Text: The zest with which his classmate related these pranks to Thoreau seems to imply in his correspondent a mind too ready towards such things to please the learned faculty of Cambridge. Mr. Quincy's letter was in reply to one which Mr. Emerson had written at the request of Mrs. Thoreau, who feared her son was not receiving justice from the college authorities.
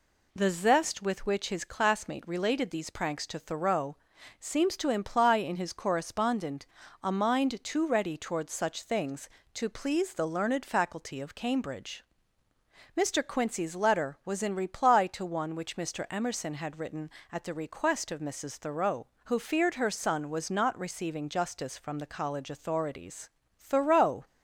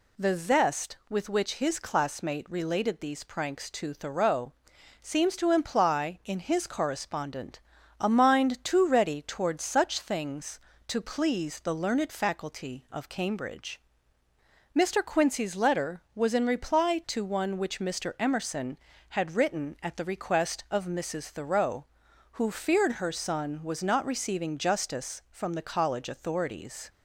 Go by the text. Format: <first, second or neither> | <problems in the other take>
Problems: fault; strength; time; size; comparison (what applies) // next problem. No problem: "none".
second | pauses between "Thoreau" and "seems"; at 3.9 s; 0.42 s long; noticeable in the second // pauses between "correspondent" and "a"; slight; at 6.6 s; 0.36 s long; also in the second // goes on to say "Thoreau"; noticeable; from 23.5 s on; 0.66 s long